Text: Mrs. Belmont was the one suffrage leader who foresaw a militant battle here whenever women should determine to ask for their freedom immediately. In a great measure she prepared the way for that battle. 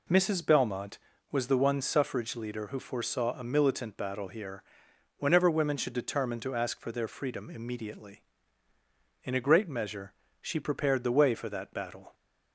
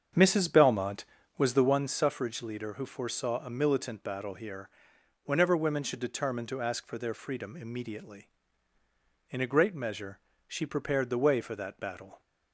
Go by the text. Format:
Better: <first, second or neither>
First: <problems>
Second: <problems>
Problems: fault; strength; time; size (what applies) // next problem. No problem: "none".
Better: first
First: pauses between "here" and "whenever"; noticeable; at 4.6 s; 0.56 s long // pauses between "measure" and "she"; slight; at 10.1 s; 0.26 s long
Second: starts louder than the rest; strong; until 1.8 s; 7.5 dB // pauses between "here" and "whenever"; noticeable; at 4.6 s; 0.56 s long // pauses between "measure" and "she"; slight; at 10.1 s; 0.26 s long